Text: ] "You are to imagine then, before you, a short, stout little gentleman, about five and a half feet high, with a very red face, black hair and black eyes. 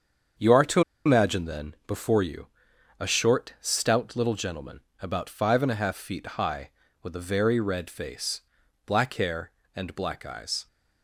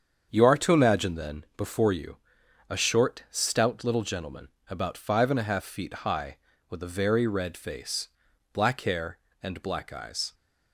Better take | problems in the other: second | starts louder than the rest; strong; until 1.6 s; 7.5 dB; strong in the second // pauses between "to" and "imagine"; slight; at 0.8 s; 0.25 s long

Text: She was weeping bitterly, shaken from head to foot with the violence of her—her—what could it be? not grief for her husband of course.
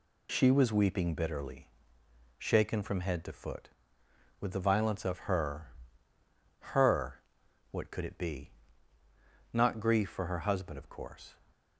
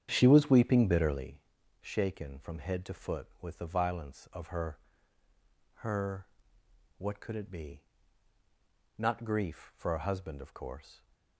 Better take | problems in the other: first | starts louder than the rest; strong; until 1.3 s; 8.5 dB

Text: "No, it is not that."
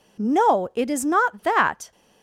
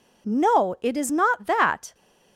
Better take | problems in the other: neither | none

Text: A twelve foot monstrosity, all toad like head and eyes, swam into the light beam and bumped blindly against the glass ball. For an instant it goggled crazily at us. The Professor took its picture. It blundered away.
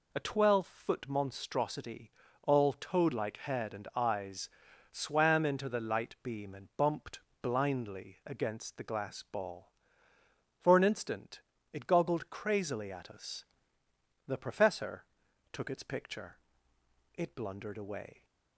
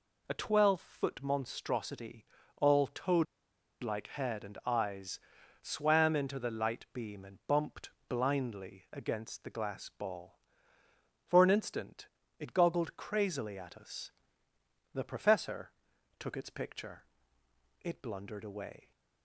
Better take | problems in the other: first | pauses between "toad" and "like"; noticeable; at 3.2 s; 0.57 s long // pauses between "bumped" and "blindly"; slight; at 7.9 s; 0.18 s long; slight in the first // pauses between "instant" and "it"; slight; at 12.0 s; 0.32 s long; slight in the first // pauses between "Professor" and "took"; noticeable; at 15.6 s; 0.50 s long; noticeable in the first

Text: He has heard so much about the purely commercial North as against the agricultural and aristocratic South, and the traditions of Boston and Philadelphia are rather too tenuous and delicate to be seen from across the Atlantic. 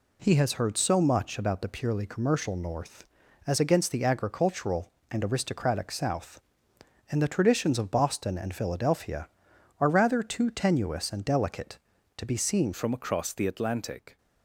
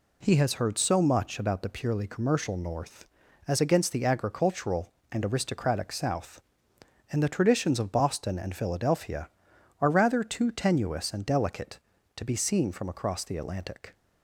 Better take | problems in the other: second | changes voice at "from"; from 12.7 s on; 1.4 s long

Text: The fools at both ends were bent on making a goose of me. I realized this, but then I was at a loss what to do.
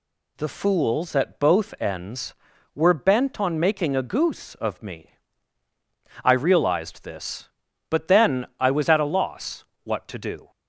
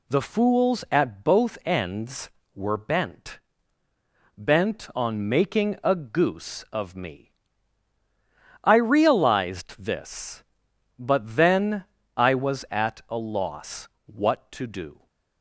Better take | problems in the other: first | says "bent" twice; at 4.3 s // pauses between "then" and "I"; slight; at 11.8 s; 0.30 s long // pauses between "loss" and "what"; slight; at 13.8 s; 0.16 s long; slight in the first

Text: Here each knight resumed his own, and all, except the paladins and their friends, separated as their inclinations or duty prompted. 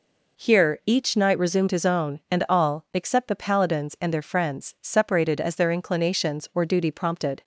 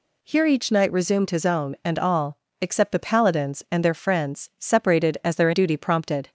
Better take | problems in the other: first | skips "inclinations or"; at 5.5 s

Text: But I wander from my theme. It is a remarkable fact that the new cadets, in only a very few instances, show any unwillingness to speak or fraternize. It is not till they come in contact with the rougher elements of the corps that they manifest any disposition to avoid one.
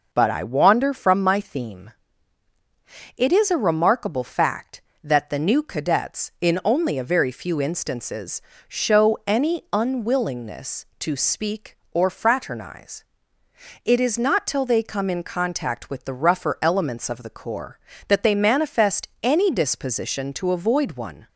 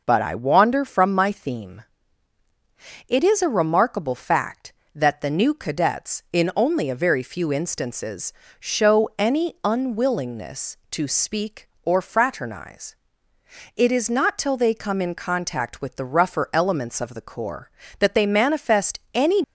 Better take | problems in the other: first | stops before "disposition to avoid one"; at 19.4 s

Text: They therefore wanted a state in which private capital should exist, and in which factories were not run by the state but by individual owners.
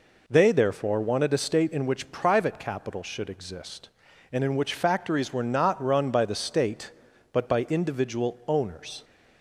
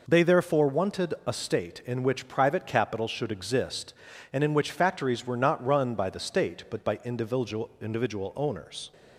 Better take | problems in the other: first | says "individual" twice; at 7.7 s

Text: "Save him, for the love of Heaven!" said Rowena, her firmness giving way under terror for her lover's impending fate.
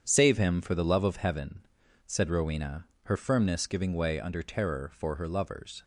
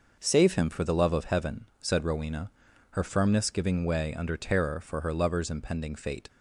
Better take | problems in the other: second | starts louder than the rest; strong; until 1.0 s; 8 dB // stops before "impending fate"; at 5.8 s

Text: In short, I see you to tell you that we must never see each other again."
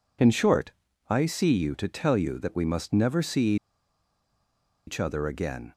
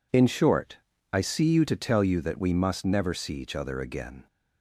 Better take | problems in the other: second | pauses between "see" and "each"; strong; at 3.5 s; 1.3 s long

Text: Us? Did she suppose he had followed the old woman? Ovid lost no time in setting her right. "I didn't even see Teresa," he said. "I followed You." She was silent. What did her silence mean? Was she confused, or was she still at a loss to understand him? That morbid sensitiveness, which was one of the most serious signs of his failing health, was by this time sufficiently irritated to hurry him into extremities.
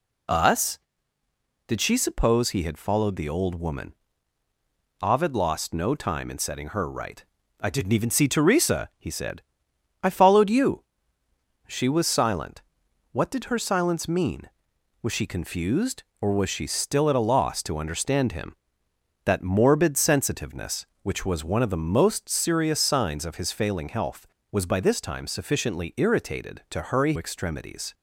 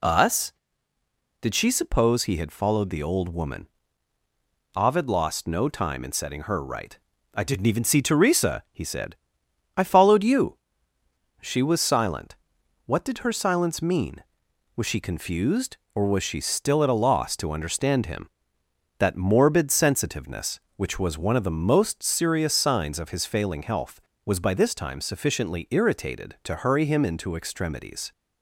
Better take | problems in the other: second | skips "him into"; at 27.1 s

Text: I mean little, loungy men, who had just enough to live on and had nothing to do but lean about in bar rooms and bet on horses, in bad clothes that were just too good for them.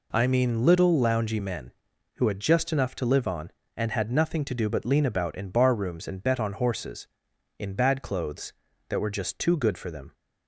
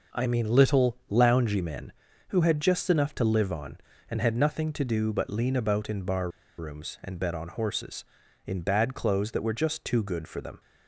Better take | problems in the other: first | pauses between "bar" and "rooms"; slight; at 6.2 s; 0.29 s long

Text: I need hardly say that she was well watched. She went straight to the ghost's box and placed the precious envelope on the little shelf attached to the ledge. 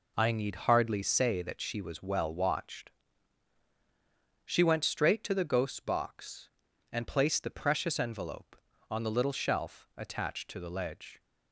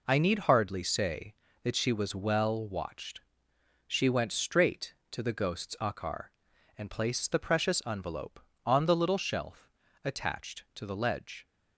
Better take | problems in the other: first | says "akar" for "box"; at 5.8 s // pauses between "shelf" and "attached"; slight; at 9.7 s; 0.34 s long

